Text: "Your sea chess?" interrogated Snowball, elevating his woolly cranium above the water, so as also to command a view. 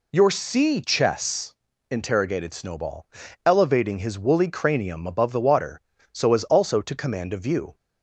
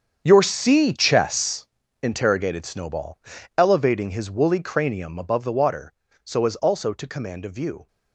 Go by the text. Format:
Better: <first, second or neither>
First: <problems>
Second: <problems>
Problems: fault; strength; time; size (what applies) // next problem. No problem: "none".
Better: first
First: none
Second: gets quieter; strong; throughout; 14.5 dB